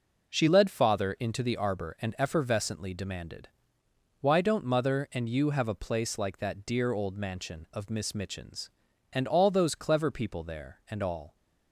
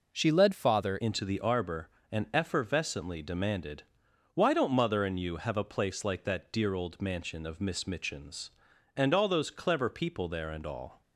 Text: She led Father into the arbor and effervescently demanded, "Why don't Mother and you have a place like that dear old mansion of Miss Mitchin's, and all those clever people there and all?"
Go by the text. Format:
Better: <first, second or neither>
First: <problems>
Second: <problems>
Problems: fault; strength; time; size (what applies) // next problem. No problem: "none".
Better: first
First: none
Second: changes voice at "into"; from 0.9 s on; 10.1 s long